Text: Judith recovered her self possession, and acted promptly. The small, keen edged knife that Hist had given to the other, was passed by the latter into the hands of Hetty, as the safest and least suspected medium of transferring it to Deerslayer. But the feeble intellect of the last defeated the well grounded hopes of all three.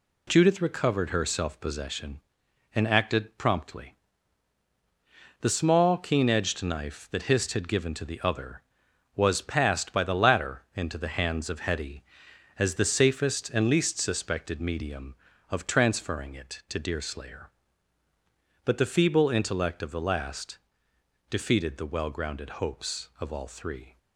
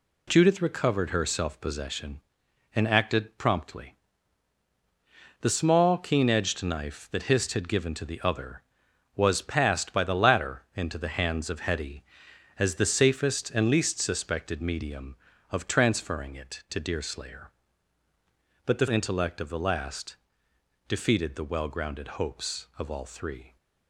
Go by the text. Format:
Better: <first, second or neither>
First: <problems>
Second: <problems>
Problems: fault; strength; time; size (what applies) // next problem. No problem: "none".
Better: first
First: pauses between "last" and "defeated"; noticeable; at 20.5 s; 0.72 s long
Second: skips "feeble"; at 18.8 s // pauses between "last" and "defeated"; noticeable; at 20.1 s; 0.72 s long